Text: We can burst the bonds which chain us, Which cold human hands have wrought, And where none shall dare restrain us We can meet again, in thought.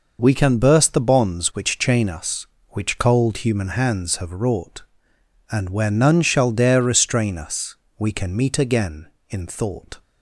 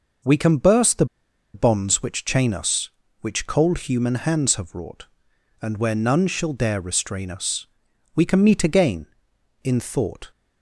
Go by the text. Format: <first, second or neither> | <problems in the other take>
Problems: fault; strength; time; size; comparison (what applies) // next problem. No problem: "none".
first | pauses between "the" and "bonds"; noticeable; at 1.0 s; 0.47 s long // pauses between "us" and "We"; noticeable; at 7.6 s; 0.48 s long; slight in the first